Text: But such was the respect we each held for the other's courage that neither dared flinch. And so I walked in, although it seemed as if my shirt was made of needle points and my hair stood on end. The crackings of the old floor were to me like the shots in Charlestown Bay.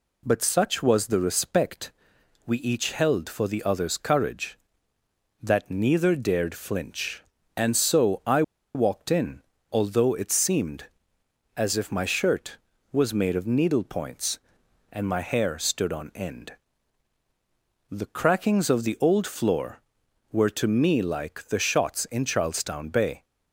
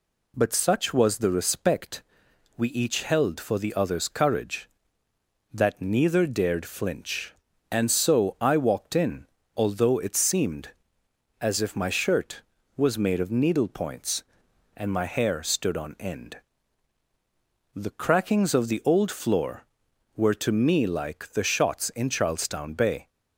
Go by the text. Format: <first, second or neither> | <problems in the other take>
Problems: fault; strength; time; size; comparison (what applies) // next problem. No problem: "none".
second | pauses between "respect" and "we"; noticeable; at 1.9 s; 0.54 s long; noticeable in the second // pauses between "I" and "walked"; slight; at 8.4 s; 0.32 s long